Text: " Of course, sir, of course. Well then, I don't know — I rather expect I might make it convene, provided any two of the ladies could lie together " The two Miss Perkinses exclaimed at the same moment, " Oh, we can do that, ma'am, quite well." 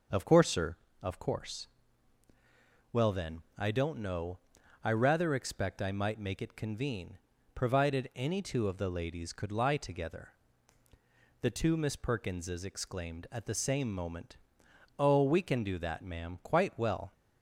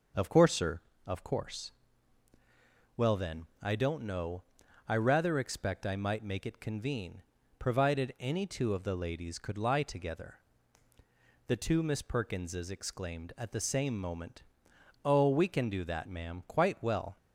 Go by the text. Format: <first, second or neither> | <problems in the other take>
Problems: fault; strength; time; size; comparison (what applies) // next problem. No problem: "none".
neither | starts louder than the rest; the same in both